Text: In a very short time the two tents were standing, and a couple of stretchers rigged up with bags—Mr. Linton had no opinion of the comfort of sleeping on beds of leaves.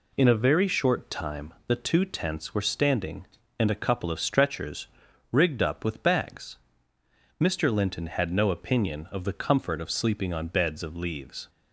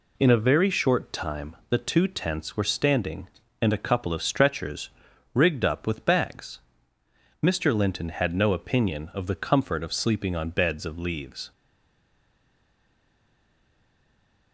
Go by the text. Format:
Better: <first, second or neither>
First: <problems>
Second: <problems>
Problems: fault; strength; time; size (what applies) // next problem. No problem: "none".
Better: first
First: pauses between "stretchers" and "rigged"; at 4.8 s; 0.44 s long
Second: pauses between "stretchers" and "rigged"; at 4.8 s; 0.44 s long // stays silent after the last word; strong; from 11.5 s on; 3.0 s long